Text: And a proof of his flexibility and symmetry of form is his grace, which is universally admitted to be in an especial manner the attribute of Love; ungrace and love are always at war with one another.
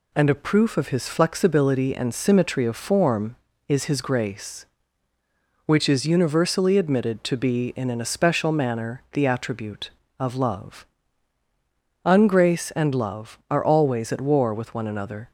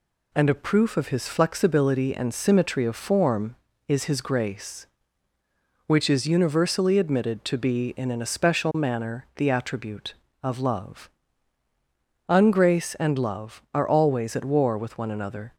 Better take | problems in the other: neither | none

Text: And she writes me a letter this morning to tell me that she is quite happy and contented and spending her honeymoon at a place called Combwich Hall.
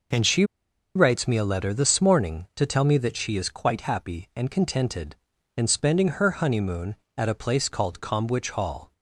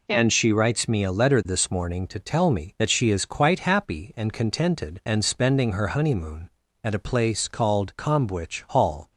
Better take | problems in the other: second | pauses between "she" and "writes"; noticeable; at 0.4 s; 0.51 s long

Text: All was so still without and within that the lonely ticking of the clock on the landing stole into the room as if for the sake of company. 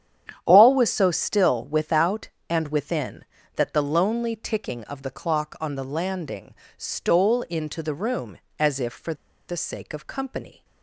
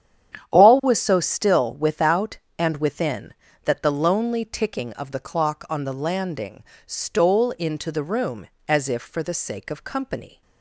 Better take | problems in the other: second | starts louder than the rest; strong; until 1.4 s; 9.5 dB; strong in the second // pauses between "landing" and "stole"; slight; at 6.5 s; 0.24 s long; slight in the second // pauses between "for" and "the"; slight; at 9.1 s; 0.34 s long

